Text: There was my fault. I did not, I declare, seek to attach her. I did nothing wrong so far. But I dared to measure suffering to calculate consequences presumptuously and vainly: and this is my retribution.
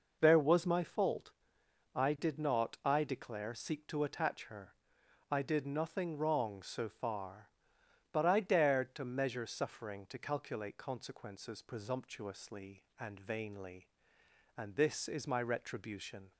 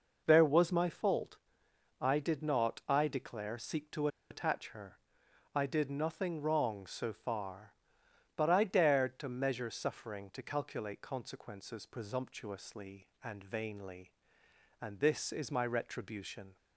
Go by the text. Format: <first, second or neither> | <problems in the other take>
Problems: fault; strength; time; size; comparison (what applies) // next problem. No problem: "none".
first | pauses between "to" and "attach"; slight; at 4.0 s; 0.23 s long